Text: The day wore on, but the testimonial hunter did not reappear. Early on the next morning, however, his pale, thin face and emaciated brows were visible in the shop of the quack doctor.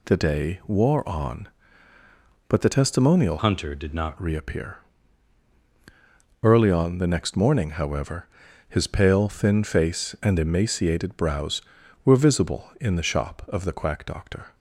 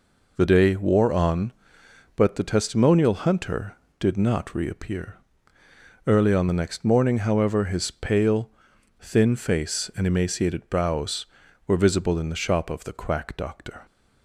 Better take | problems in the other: second | changes voice from "hunter" to "not"; from 3.3 to 4.1 s; 0.8 s long

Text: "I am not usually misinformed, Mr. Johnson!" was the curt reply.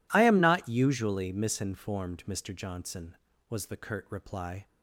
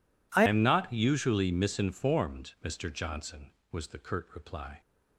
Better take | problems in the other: first | changes voice at "am"; from 0.4 s on; 4.4 s long

